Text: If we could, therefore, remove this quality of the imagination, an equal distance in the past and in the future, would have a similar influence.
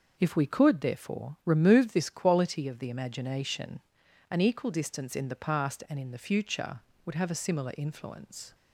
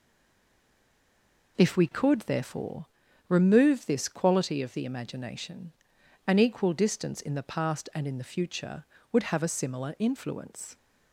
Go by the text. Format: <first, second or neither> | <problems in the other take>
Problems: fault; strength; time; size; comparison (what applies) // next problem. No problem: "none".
first | stays silent before the first word; noticeable; until 1.5 s; 1.5 s long